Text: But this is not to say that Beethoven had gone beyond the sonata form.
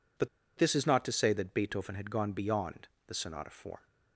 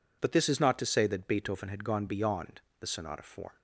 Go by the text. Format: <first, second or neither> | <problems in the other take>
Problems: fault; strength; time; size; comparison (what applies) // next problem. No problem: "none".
second | pauses between "But" and "this"; slight; at 0.2 s; 0.31 s long // pauses between "beyond" and "the"; slight; at 2.8 s; 0.20 s long; slight in the second